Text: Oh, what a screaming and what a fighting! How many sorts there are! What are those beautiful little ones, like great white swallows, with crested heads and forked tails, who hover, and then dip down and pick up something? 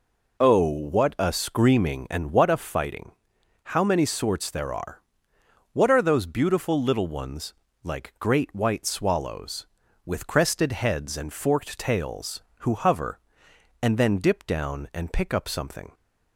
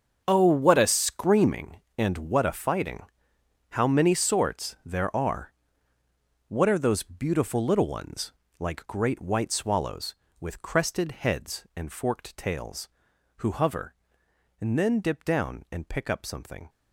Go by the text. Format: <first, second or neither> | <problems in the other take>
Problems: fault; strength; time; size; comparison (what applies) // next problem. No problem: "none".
first | gets quieter; strong; throughout; 13.5 dB